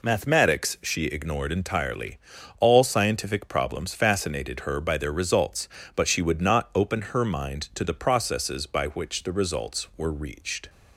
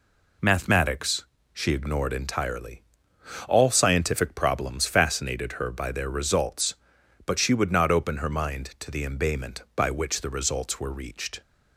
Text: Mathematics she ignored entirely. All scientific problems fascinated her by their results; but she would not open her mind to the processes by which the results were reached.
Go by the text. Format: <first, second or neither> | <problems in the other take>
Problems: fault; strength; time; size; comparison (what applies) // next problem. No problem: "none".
first | pauses between "Mathematics" and "she"; slight; at 1.2 s; 0.26 s long // says "embayment" for "processes"; at 9.0 s